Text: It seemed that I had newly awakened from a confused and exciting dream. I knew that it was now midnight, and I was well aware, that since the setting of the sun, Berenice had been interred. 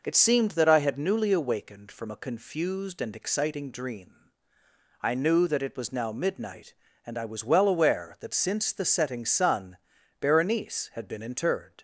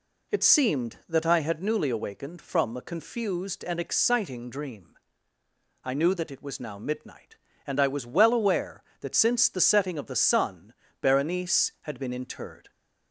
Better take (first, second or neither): second